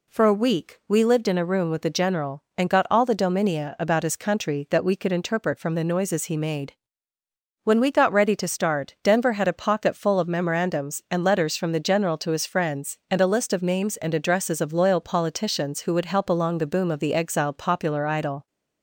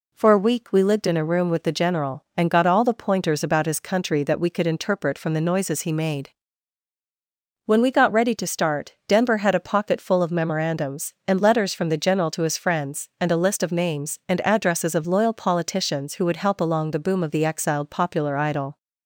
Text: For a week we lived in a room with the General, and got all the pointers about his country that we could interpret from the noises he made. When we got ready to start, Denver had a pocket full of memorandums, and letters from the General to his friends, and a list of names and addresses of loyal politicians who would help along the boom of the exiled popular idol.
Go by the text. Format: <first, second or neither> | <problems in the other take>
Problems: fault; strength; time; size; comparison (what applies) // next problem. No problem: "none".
second | says "dominia" for "pointers"; at 3.1 s